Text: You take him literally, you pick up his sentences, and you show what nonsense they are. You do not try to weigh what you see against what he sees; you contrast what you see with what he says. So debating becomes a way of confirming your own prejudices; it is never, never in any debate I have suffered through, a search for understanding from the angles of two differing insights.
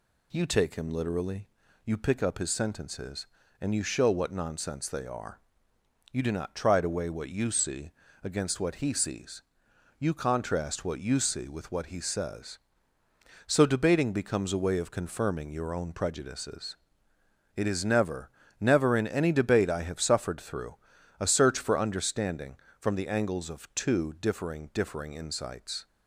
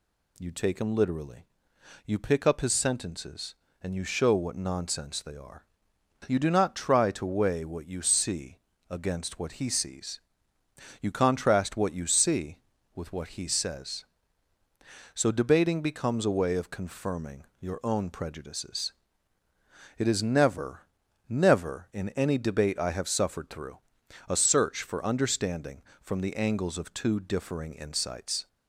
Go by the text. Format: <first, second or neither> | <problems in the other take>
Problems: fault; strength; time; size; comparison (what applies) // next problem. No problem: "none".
second | pauses between "see" and "against"; slight; at 7.9 s; 0.32 s long; slight in the second // says "differing" twice; at 24.7 s